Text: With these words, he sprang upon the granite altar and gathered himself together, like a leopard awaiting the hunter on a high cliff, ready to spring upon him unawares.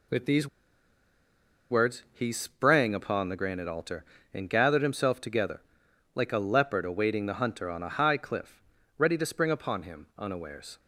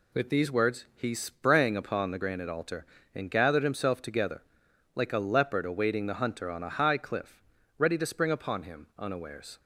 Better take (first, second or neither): second